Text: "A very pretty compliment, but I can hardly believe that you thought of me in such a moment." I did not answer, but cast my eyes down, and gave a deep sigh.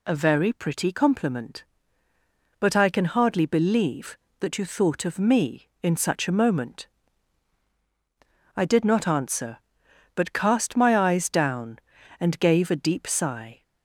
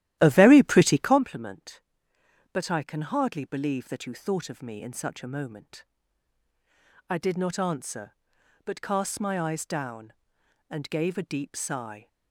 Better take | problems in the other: first | starts louder than the rest; strong; until 1.2 s; 13.5 dB

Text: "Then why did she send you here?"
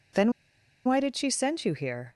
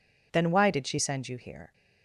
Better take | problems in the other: second | pauses between "Then" and "why"; noticeable; at 0.3 s; 0.53 s long

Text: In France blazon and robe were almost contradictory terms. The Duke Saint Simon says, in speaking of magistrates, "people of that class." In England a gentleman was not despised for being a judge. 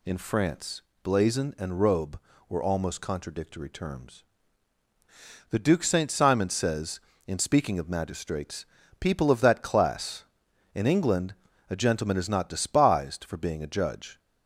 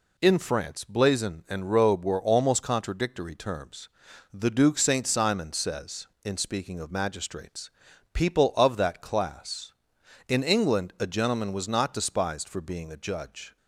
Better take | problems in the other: second | pauses between "France" and "blazon"; slight; at 0.8 s; 0.22 s long // pauses between "England" and "a"; slight; at 11.3 s; 0.34 s long // says "is" for "was"; at 12.1 s

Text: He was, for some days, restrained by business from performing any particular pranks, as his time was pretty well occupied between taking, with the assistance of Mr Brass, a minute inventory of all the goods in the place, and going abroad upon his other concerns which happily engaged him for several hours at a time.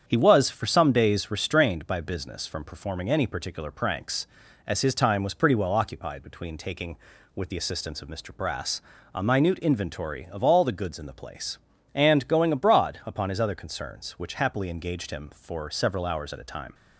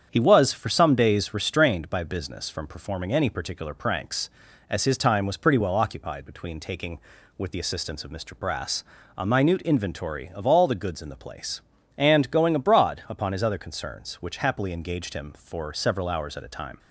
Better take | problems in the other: neither | starts louder than the rest; strong; the same in both

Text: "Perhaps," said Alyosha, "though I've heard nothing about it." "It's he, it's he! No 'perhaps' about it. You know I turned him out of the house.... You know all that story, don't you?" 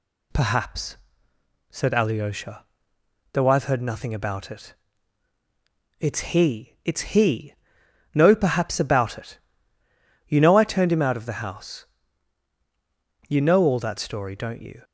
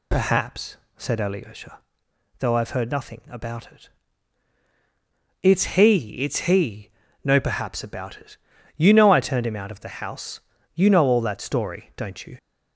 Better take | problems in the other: neither | none

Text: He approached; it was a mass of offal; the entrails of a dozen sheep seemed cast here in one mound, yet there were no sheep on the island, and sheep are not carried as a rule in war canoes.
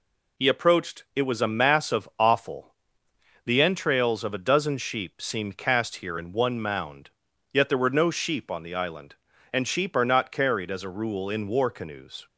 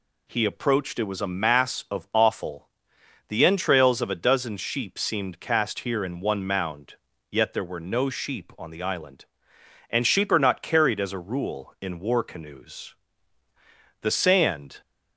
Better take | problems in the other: first | goes on to say "The sand"; noticeable; from 14.0 s on; 0.80 s long

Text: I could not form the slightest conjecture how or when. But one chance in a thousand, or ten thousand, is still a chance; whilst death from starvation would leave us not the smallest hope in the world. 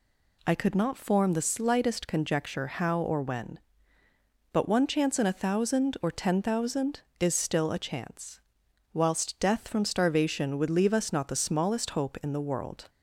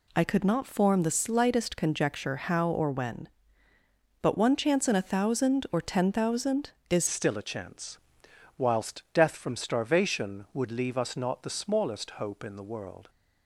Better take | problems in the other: first | changes voice at "still"; from 7.0 s on; 6.0 s long

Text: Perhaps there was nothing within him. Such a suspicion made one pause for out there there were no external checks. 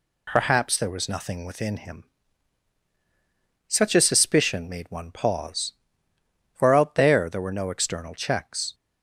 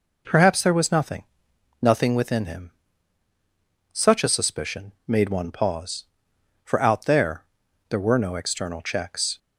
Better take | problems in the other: first | says "nothing" twice; at 1.7 s // pauses between "there" and "there"; noticeable; at 7.4 s; 0.46 s long

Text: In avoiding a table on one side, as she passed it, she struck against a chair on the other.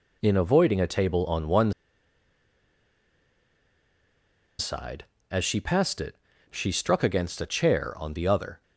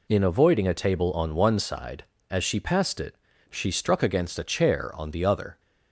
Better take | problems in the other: second | pauses between "one" and "side"; strong; at 1.7 s; 2.8 s long

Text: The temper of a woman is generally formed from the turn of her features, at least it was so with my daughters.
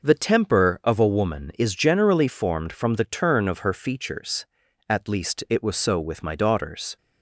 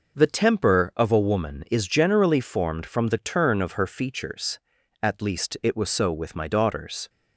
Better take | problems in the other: neither | none

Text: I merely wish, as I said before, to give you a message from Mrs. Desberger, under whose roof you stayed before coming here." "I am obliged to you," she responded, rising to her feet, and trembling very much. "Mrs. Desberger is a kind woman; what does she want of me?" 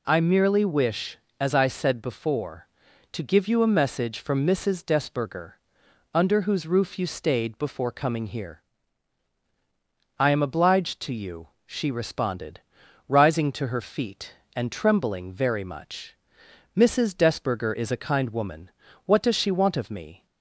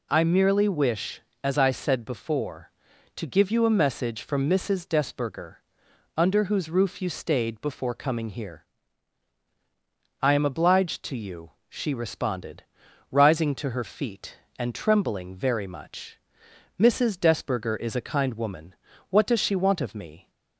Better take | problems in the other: neither | none

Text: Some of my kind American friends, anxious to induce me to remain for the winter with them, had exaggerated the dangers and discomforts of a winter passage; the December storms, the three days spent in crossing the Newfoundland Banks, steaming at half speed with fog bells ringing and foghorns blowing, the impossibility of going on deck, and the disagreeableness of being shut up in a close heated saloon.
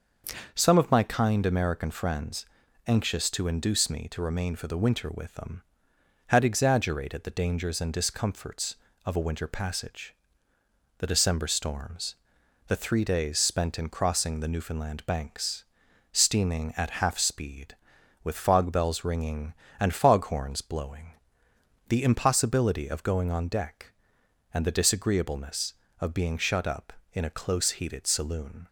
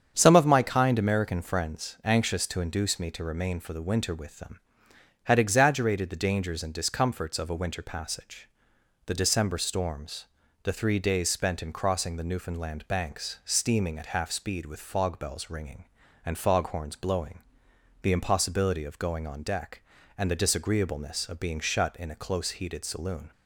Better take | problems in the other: first | starts louder than the rest; strong; until 1.1 s; 7.5 dB; noticeable in the first // skips "up"; at 21.9 s

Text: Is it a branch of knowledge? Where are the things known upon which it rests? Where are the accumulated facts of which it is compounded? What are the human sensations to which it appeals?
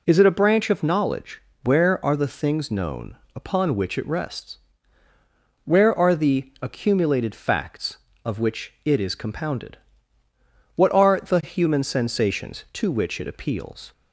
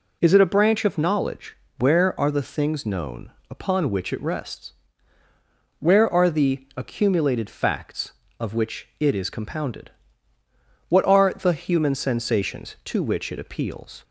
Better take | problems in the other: neither | pauses between "known" and "upon"; slight; the same in both

